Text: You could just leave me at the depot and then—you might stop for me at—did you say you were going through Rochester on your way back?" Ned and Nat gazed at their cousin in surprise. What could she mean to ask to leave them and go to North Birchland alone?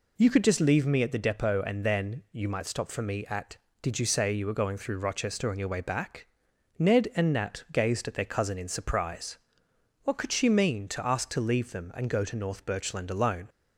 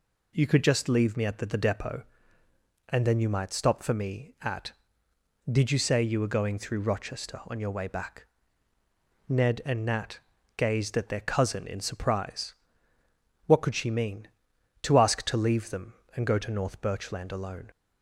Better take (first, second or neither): first